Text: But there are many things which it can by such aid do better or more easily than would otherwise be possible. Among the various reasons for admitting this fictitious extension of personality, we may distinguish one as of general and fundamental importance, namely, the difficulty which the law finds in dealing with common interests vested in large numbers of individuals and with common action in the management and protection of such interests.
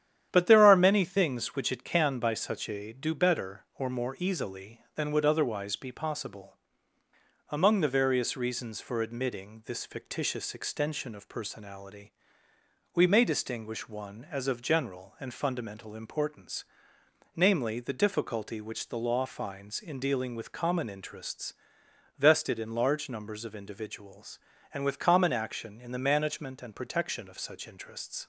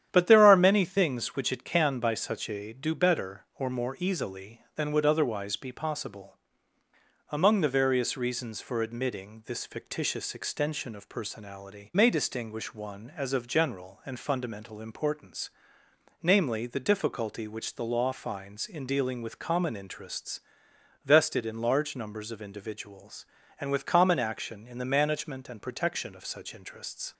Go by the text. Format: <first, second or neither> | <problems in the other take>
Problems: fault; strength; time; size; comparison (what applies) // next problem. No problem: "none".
first | starts louder than the rest; strong; until 1.1 s; 10 dB; strong in the first // skips "we"; at 11.9 s // pauses between "interests" and "vested"; noticeable; at 20.3 s; 0.66 s long; noticeable in the first